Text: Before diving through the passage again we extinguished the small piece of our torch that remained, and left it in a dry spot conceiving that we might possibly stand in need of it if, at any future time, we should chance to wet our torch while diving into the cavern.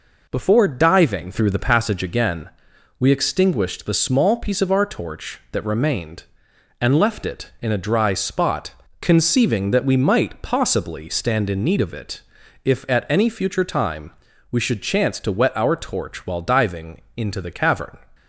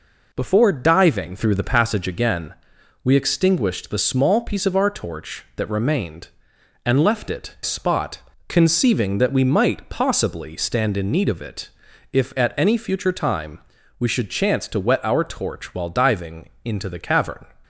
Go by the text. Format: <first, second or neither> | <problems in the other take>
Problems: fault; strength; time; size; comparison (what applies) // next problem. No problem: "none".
first | pauses between "again" and "we"; noticeable; at 2.5 s; 0.50 s long; noticeable in the first // skips "in a dry"; at 7.5 s // pauses between "spot" and "conceiving"; slight; at 8.2 s; 0.26 s long; slight in the first // pauses between "it" and "if"; at 11.7 s; 0.42 s long; also in the first